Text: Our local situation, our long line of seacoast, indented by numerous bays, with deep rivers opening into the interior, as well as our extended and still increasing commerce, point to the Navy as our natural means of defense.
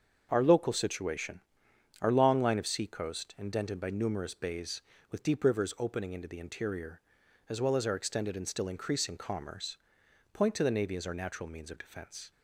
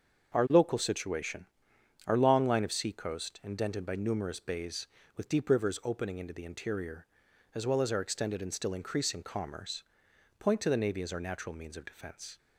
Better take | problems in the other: neither | starts louder than the rest; the same in both

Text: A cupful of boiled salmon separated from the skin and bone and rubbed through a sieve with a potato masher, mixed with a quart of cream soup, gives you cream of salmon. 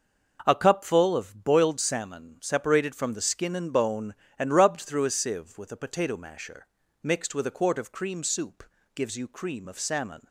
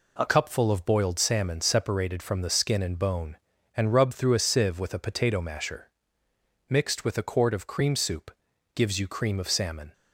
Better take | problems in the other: first | changes voice at "cupful"; from 0.2 s on; 9.7 s long

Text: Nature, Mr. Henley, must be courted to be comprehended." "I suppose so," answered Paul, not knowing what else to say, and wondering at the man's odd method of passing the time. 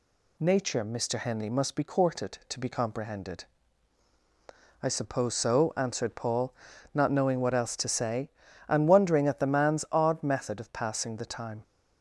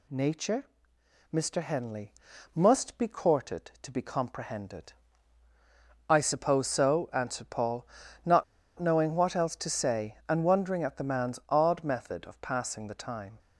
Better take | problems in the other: first | pauses between "not" and "knowing"; slight; at 8.4 s; 0.34 s long

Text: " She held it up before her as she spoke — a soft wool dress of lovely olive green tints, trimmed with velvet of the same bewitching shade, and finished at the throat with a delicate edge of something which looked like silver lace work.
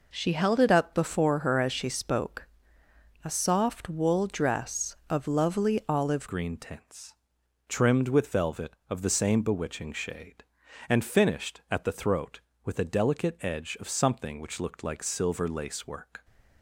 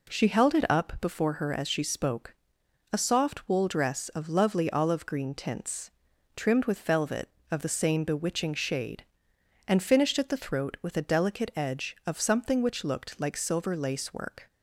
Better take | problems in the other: second | changes voice at "green"; from 6.2 s on; 10.0 s long

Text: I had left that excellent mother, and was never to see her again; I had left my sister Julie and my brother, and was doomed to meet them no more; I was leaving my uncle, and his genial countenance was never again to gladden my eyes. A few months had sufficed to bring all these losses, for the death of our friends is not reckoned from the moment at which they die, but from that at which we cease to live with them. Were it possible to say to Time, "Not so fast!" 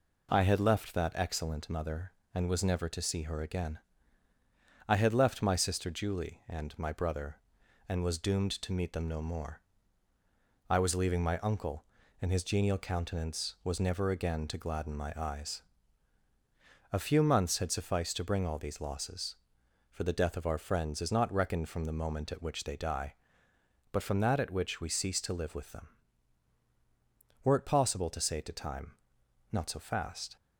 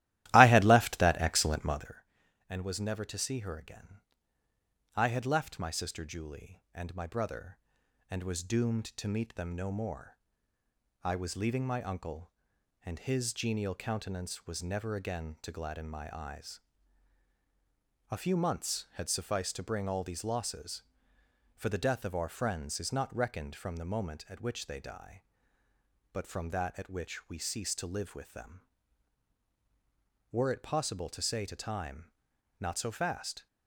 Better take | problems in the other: first | starts louder than the rest; strong; until 2.0 s; 15 dB

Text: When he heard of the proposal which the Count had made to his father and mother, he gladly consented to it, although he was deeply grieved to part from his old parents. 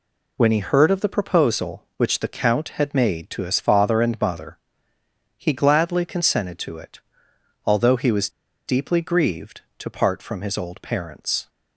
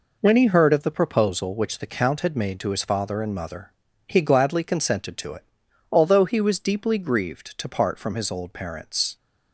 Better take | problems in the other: second | pauses between "was" and "deeply"; at 8.2 s; 0.38 s long

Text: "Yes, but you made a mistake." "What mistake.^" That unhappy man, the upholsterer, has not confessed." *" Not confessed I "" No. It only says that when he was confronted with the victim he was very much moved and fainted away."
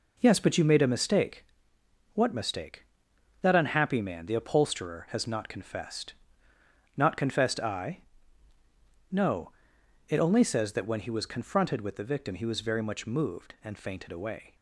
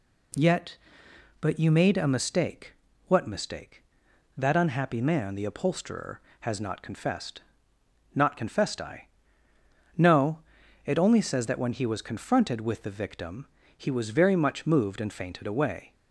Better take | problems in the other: first | says "Yet" for "Yes"; at 0.3 s // pauses between "victim" and "he"; slight; at 13.4 s; 0.30 s long

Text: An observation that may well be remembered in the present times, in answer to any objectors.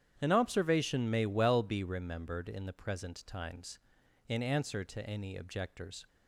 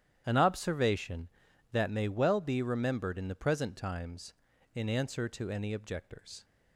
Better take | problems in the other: second | starts louder than the rest; strong; until 1.1 s; 9.5 dB; strong in the second // skips "that"; at 1.1 s

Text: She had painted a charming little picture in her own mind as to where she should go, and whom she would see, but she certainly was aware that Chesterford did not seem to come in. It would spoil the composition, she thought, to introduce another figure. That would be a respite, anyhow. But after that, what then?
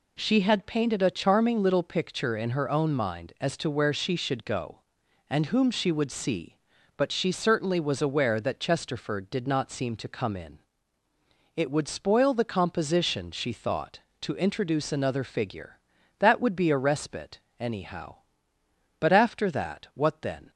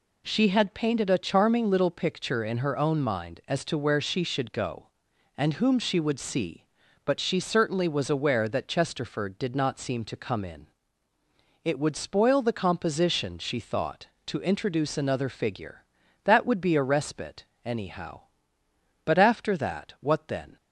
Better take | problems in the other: neither | none

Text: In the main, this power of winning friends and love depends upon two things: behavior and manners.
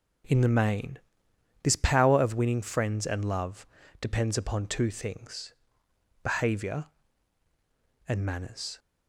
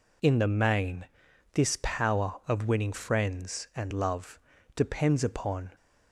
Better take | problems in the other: first | pauses between "love" and "depends"; at 4.3 s; 0.38 s long; slight in the first // stops before "two things behavior and manners"; at 5.7 s

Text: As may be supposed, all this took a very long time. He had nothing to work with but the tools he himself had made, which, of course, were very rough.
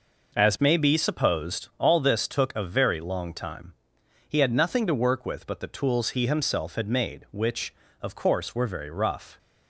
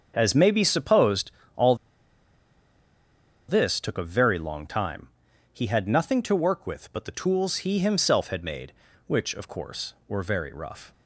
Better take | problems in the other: first | starts louder than the rest; until 1.1 s; 7 dB // pauses between "all" and "this"; strong; at 1.7 s; 1.7 s long

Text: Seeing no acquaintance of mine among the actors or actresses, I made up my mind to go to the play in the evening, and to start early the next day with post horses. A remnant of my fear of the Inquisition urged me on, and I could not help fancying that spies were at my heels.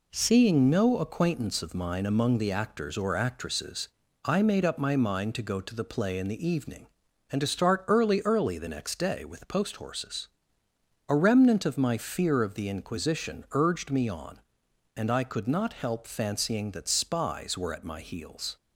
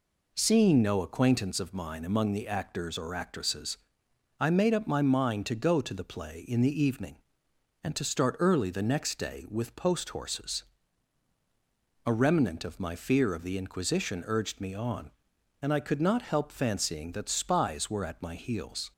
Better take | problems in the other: second | says "early" twice; at 8.2 s

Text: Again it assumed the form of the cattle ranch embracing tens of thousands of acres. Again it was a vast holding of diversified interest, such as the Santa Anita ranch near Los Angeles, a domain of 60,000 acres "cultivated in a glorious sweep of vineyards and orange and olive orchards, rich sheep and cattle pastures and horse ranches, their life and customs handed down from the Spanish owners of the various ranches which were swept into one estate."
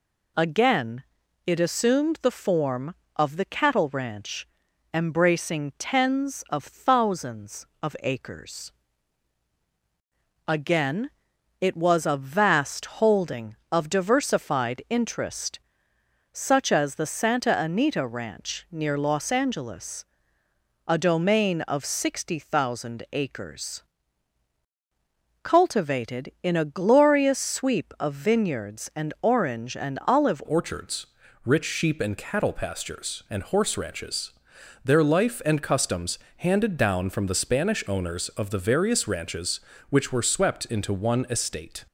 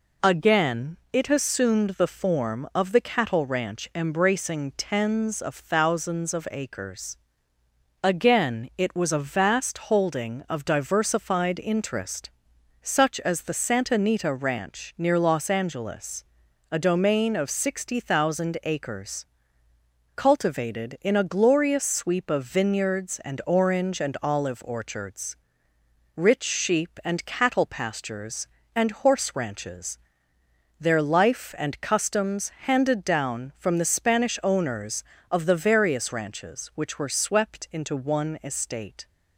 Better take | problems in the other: second | pauses between "Again" and "it"; at 1.0 s; 0.42 s long; slight in the second // pauses between "ranch" and "embracing"; at 4.4 s; 0.44 s long // pauses between "Again" and "it"; noticeable; at 11.1 s; 0.50 s long // pauses between "acres" and "cultivated"; strong; at 23.8 s; 1.6 s long; noticeable in the second // changes voice at "orchards"; from 30.4 s on; 11.4 s long // pauses between "customs" and "handed"; slight; at 36.1 s; 0.20 s long

